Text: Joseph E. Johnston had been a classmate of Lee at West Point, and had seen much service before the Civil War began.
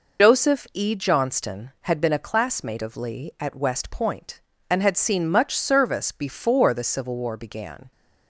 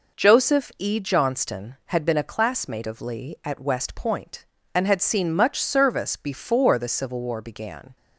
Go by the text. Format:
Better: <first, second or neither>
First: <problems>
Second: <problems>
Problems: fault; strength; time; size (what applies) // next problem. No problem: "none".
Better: second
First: loses the start of "Joseph"; at 0.1 s; 90 ms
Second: none